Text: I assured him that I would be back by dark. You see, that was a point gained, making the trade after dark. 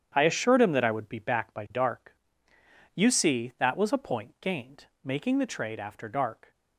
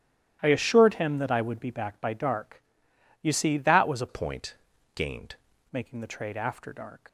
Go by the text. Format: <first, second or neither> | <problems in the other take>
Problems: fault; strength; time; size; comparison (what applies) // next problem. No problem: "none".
first | starts louder than the rest; strong; until 1.4 s; 12.5 dB; strong in the first // changes voice from "point" to "gained"; from 4.0 to 5.3 s; 1.3 s long // pauses between "point" and "gained"; at 4.5 s; 0.40 s long